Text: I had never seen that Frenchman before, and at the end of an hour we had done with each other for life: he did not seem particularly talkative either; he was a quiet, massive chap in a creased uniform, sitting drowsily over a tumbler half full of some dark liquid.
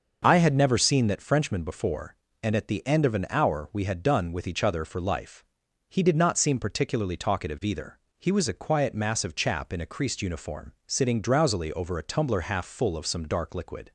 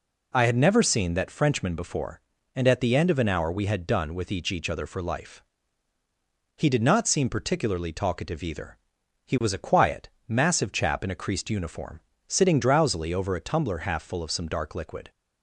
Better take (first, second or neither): first